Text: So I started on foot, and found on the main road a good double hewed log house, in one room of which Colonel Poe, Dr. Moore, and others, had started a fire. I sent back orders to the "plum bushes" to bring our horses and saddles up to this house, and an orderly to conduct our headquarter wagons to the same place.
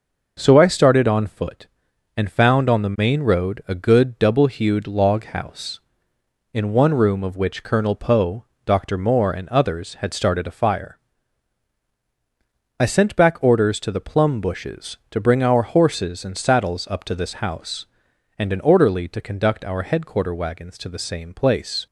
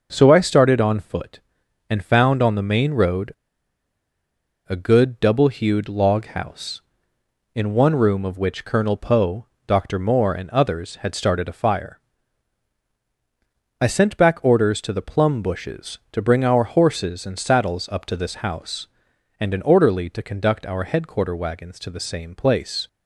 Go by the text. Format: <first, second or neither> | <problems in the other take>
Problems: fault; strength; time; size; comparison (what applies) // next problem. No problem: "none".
first | pauses between "road" and "a"; strong; at 3.3 s; 1.3 s long